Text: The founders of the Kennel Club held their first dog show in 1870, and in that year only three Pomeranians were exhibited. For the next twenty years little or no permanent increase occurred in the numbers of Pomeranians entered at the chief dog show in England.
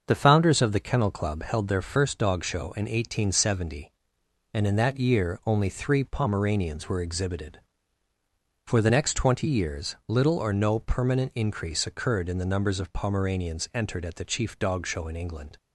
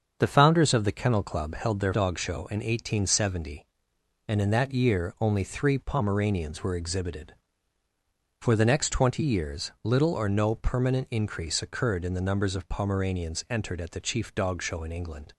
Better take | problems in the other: first | starts louder than the rest; until 1.1 s; 7 dB; also in the first // skips "first"; at 1.9 s

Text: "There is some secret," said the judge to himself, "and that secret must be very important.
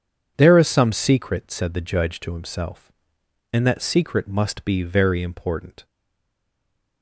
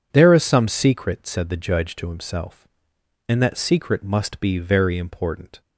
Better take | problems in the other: second | stays silent after the last word; noticeable; from 5.8 s on; 1.2 s long

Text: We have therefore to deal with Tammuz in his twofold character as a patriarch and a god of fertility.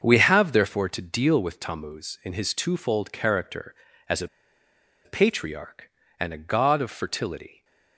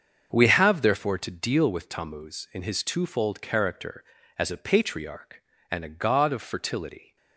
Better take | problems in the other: second | starts louder than the rest; until 1.0 s; 7 dB; also in the second // pauses between "a" and "patriarch"; noticeable; at 4.2 s; 0.78 s long

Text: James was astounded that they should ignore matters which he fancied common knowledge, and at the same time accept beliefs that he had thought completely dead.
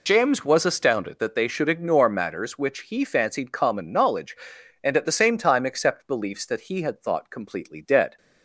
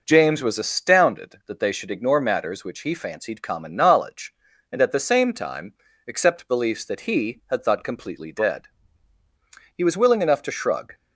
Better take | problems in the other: first | pauses between "time" and "accept"; slight; at 5.7 s; 0.34 s long // goes on to say "He was willing enough to shrug"; noticeable; from 9.7 s on; 1.1 s long

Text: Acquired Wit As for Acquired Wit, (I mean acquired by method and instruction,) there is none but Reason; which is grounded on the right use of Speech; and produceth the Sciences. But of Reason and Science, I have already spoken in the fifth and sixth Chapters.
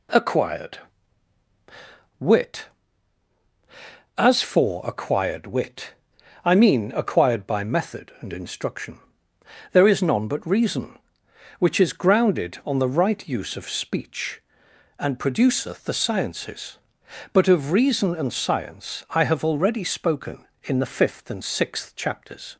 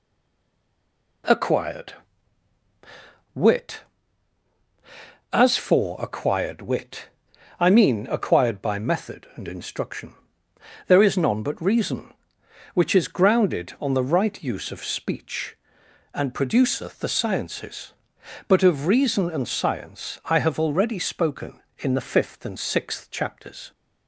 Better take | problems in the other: first | stays silent before the first word; noticeable; until 1.2 s; 1.2 s long // pauses between "Acquired" and "Wit"; strong; at 1.9 s; 1.4 s long; strong in the first

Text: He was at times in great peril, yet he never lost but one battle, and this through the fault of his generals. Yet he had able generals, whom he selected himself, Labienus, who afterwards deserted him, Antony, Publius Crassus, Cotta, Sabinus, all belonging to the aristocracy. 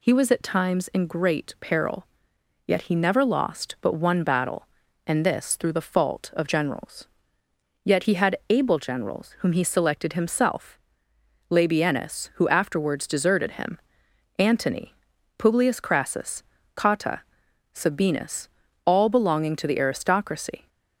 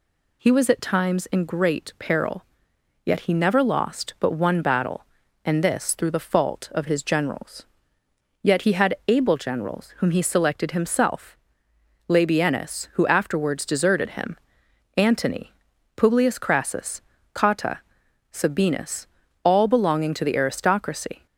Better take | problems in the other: second | skips "his"; at 6.4 s

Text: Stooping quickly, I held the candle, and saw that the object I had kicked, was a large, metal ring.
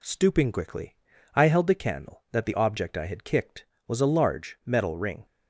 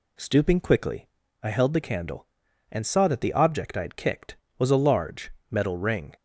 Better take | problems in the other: second | skips "and saw"; at 2.2 s

